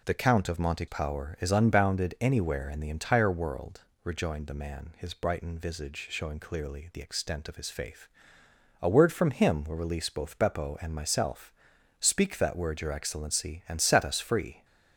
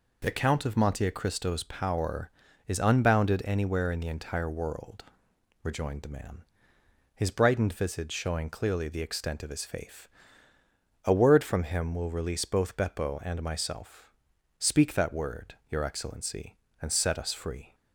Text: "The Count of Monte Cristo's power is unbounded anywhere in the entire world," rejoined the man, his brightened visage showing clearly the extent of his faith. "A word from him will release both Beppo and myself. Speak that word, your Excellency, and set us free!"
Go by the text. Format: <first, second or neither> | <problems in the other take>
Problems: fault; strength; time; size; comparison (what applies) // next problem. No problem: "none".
second | skips "Cristo's"; at 0.8 s